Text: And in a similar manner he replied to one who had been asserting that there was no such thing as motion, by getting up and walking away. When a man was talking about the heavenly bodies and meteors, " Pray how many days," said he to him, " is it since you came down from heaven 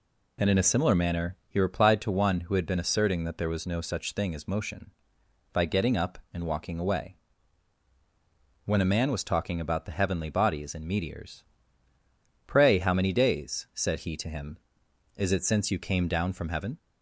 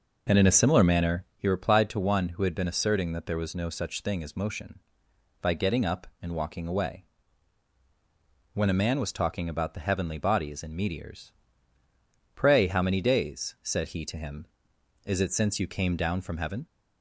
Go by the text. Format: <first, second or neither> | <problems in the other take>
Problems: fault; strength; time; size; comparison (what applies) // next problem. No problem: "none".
first | starts louder than the rest; noticeable; until 1.3 s; 5.5 dB